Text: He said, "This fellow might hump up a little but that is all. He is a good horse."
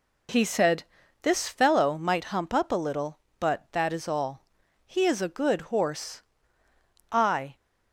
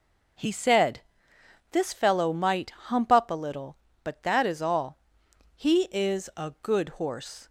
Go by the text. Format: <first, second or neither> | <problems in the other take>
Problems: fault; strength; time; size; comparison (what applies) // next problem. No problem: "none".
second | goes on to say "I"; slight; from 7.0 s on; 0.46 s long